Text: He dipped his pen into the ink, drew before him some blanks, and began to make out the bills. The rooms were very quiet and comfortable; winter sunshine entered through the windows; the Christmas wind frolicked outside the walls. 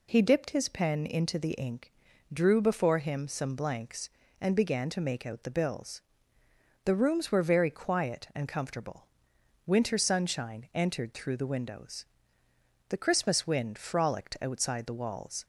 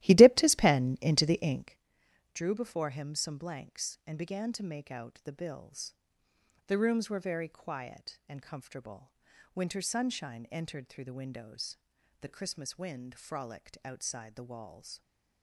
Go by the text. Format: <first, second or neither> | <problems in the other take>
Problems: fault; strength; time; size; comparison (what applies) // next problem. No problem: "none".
first | starts louder than the rest; strong; until 1.9 s; 15.5 dB